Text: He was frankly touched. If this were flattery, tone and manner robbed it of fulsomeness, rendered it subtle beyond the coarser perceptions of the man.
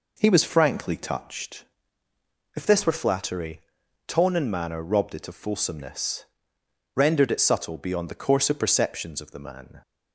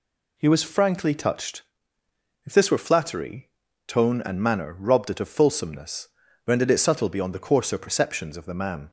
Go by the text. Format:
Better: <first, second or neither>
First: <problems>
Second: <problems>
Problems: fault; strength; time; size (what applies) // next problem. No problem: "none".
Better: second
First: starts louder than the rest; noticeable; until 1.7 s; 4.5 dB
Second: none